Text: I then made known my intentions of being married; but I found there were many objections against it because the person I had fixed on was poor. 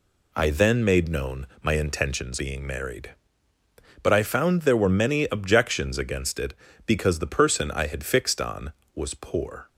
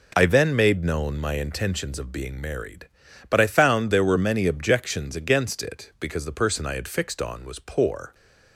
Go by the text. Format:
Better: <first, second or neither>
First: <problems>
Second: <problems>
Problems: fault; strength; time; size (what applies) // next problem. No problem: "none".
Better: second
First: pauses between "known" and "my"; slight; at 1.4 s; 0.16 s long // skips "of"; at 2.3 s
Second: none